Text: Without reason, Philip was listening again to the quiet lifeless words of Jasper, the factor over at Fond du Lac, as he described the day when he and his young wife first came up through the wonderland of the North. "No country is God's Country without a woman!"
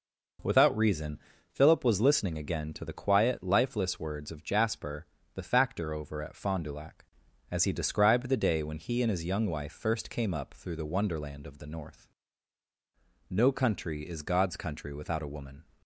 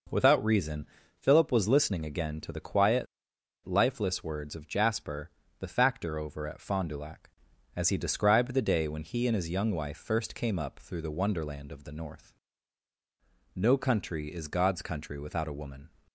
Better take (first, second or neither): first